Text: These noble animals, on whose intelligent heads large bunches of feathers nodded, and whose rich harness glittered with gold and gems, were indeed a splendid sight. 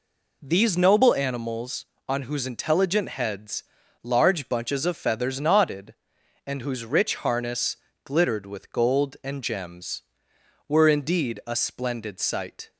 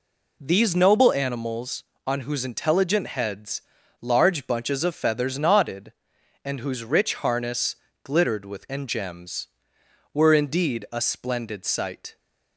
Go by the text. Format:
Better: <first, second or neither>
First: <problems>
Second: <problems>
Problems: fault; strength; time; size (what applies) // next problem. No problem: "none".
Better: first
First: pauses between "heads" and "large"; at 3.6 s; 0.40 s long // pauses between "harness" and "glittered"; slight; at 7.7 s; 0.30 s long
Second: pauses between "heads" and "large"; at 3.5 s; 0.40 s long // pauses between "harness" and "glittered"; slight; at 7.7 s; 0.30 s long // skips "gold"; at 8.6 s